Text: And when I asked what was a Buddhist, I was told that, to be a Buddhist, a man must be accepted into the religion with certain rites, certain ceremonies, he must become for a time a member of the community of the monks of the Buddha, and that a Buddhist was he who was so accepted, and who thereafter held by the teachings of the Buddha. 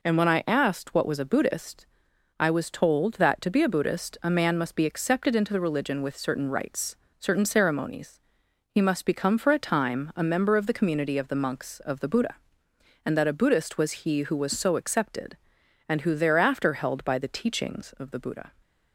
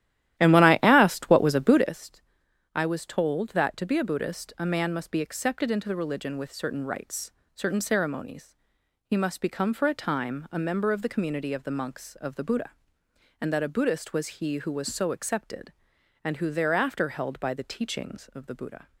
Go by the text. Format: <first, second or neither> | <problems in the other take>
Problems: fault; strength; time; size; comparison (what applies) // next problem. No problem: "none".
first | starts louder than the rest; strong; until 1.9 s; 13 dB